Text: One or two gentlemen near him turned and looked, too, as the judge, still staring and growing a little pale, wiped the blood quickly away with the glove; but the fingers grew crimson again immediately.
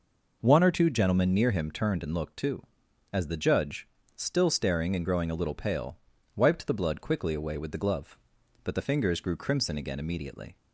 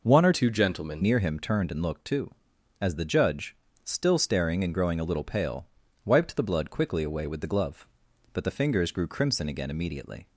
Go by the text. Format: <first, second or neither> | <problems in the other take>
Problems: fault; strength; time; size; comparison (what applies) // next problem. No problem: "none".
first | changes voice from "two" to "gentlemen"; from 0.3 to 1.0 s; 0.7 s long